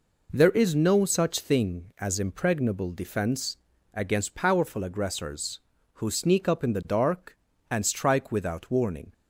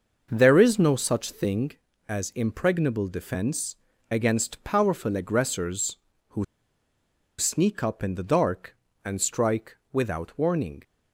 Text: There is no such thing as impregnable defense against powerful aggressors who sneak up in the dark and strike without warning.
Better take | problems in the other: first | starts louder than the rest; until 1.3 s; 6.5 dB // pauses between "defense" and "against"; slight; at 3.7 s; 0.36 s long; slight in the first // pauses between "who" and "sneak"; noticeable; at 6.4 s; 0.94 s long // pauses between "strike" and "without"; slight; at 9.7 s; 0.16 s long

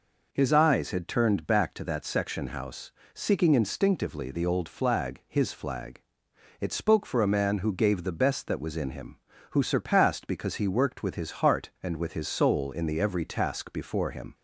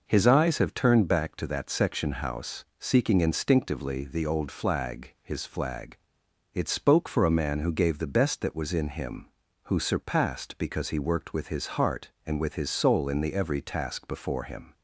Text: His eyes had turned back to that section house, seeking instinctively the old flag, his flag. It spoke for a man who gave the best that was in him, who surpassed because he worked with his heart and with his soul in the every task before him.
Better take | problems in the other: first | says "have" for "had"; at 0.5 s

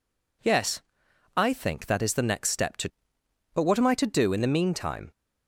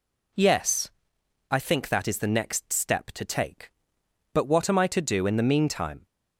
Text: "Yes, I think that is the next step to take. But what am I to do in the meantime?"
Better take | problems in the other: second | skips "take"; at 3.2 s

